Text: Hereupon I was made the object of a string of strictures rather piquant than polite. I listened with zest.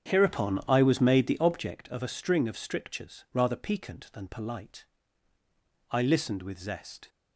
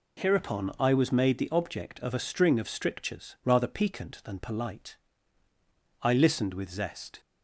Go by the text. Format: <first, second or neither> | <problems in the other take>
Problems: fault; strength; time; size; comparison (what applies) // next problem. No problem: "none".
second | starts louder than the rest; strong; until 1.8 s; 8 dB